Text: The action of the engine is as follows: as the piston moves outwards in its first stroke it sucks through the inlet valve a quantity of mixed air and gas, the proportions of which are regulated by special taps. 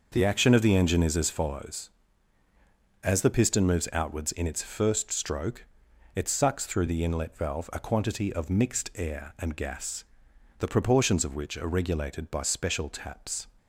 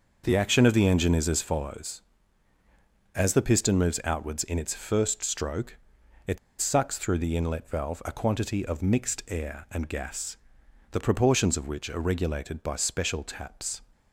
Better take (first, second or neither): first